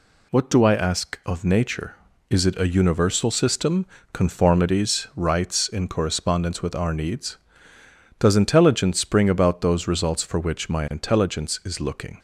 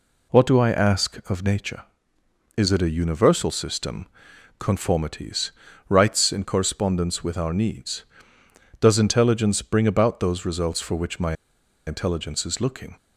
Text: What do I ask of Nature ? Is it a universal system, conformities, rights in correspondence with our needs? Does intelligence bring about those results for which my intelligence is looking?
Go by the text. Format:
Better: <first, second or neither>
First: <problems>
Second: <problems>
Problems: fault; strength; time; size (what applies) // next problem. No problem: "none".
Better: first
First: none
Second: pauses between "my" and "intelligence"; noticeable; at 11.3 s; 0.52 s long